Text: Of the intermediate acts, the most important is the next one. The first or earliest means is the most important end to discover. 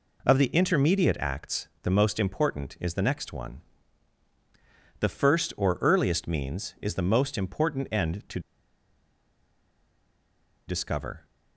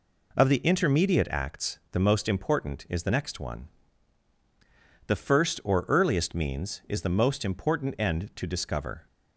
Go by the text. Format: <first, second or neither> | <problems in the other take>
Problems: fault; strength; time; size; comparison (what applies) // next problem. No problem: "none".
second | pauses between "to" and "discover"; strong; at 8.3 s; 2.2 s long